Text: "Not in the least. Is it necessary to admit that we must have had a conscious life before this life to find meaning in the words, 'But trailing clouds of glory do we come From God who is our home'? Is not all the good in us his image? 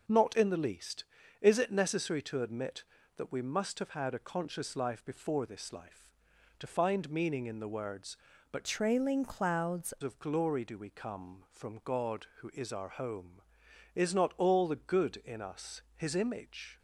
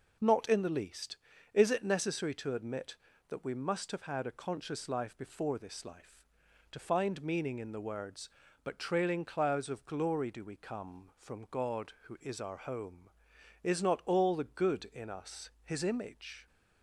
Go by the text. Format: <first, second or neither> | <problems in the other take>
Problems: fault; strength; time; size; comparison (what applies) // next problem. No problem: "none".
second | changes voice from "trailing" to "clouds"; from 8.6 to 9.9 s; 1.3 s long // pauses between "us" and "his"; slight; at 15.7 s; 0.16 s long; slight in the second